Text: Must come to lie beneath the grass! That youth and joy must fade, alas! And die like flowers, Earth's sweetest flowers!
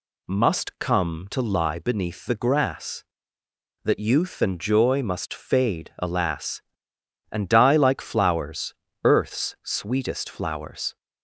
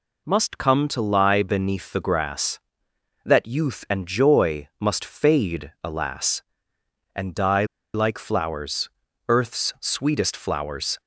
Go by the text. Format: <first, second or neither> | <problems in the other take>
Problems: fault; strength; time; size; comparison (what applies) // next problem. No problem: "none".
first | pauses between "die" and "like"; slight; at 7.6 s; 0.29 s long